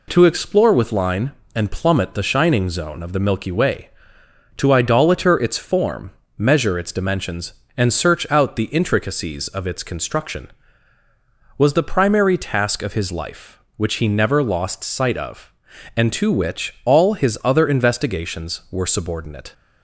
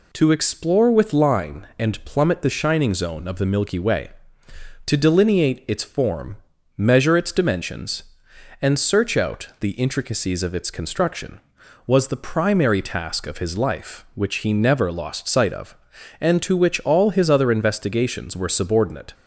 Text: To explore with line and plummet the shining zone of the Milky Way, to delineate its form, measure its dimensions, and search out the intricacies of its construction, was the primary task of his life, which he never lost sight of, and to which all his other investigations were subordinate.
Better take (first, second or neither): second